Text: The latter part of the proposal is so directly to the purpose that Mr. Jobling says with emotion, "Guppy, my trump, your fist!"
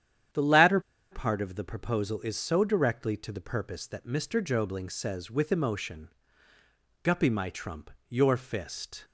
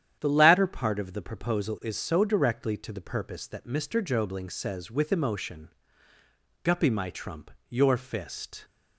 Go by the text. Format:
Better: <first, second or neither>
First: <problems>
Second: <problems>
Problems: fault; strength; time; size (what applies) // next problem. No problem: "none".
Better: second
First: starts louder than the rest; strong; until 1.6 s; 9.5 dB // pauses between "latter" and "part"; slight; at 0.7 s; 0.32 s long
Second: starts louder than the rest; strong; until 1.2 s; 9.5 dB